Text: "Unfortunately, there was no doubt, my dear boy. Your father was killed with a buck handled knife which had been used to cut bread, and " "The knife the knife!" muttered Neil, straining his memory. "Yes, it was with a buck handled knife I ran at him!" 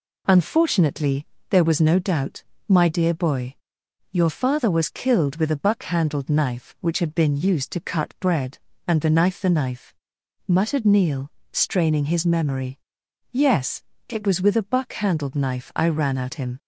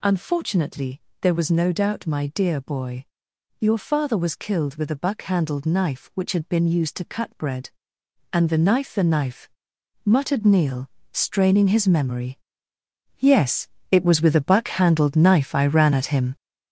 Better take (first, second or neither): first